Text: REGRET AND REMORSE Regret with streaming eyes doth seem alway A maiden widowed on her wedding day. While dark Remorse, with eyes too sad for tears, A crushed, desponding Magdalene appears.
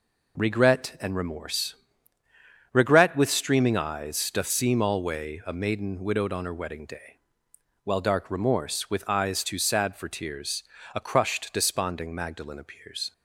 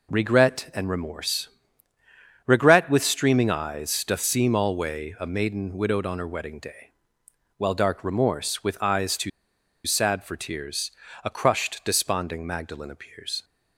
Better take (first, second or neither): first